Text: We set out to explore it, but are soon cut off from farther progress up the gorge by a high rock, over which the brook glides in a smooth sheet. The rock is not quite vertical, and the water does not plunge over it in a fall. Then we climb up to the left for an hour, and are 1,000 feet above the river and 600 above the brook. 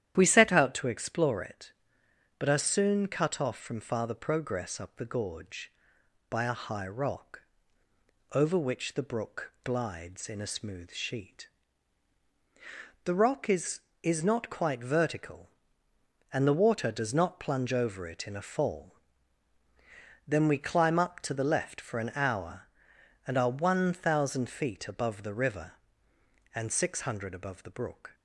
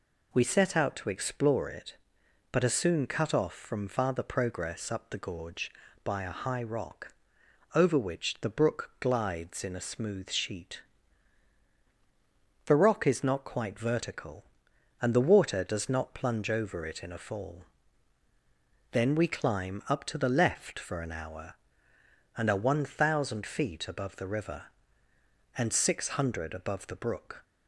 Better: second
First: starts louder than the rest; strong; until 1.1 s; 10.5 dB // says "is" twice; at 14.0 s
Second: none

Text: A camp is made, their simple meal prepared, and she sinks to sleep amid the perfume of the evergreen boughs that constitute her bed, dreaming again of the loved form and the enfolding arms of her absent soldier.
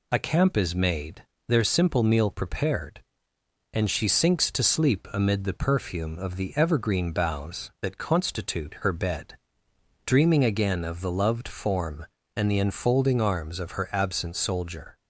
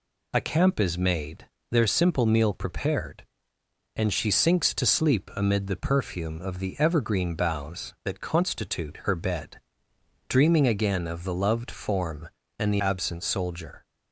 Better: first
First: none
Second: skips "enfolding arms of her"; at 12.7 s

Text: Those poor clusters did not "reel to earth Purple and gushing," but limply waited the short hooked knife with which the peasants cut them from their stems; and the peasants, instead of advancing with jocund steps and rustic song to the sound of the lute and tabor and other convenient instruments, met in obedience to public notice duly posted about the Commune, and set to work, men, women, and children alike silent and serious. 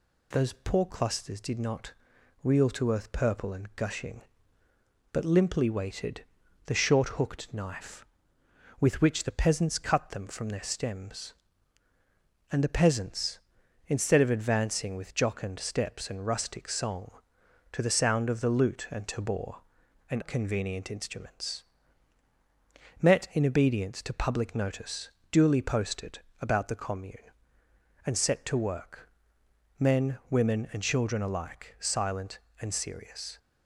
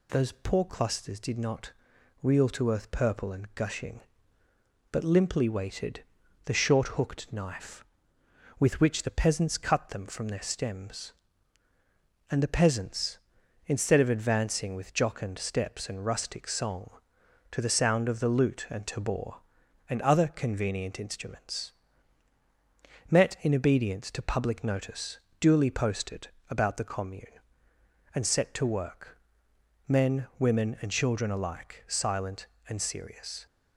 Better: second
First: pauses between "not" and "reel"; noticeable; at 1.9 s; 0.52 s long // pauses between "waited" and "the"; at 6.2 s; 0.44 s long // skips "other"; at 20.2 s // pauses between "notice" and "duly"; slight; at 25.0 s; 0.20 s long // pauses between "posted" and "about"; slight; at 26.1 s; 0.22 s long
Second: pauses between "not" and "reel"; noticeable; at 1.7 s; 0.52 s long // pauses between "waited" and "the"; at 6.0 s; 0.44 s long // pauses between "notice" and "duly"; slight; at 25.1 s; 0.20 s long // pauses between "posted" and "about"; slight; at 26.2 s; 0.22 s long

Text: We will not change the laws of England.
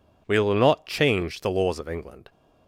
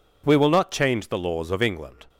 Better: neither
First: none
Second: none

